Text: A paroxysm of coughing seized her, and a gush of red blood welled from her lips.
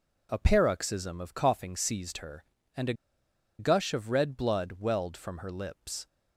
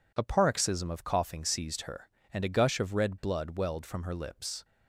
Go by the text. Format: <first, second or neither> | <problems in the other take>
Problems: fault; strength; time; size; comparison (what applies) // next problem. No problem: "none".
second | pauses between "a" and "gush"; noticeable; at 2.9 s; 0.65 s long